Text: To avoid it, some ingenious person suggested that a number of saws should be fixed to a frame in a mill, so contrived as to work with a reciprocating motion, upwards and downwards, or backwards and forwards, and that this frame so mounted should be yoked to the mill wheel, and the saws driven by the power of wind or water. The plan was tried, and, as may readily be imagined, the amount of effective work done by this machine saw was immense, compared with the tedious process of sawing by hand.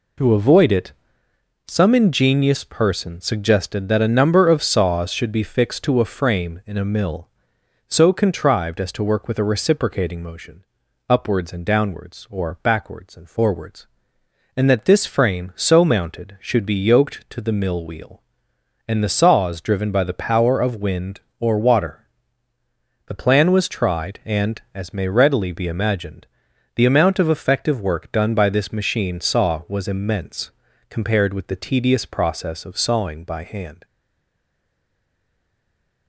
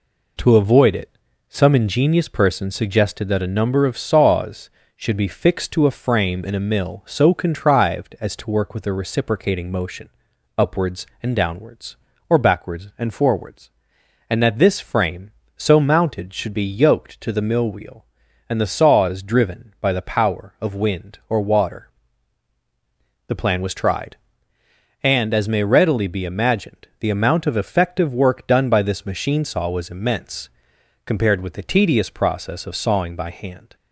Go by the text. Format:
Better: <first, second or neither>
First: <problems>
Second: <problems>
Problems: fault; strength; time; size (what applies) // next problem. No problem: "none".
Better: second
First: stays silent after the last word; from 33.8 s on; 2.2 s long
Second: none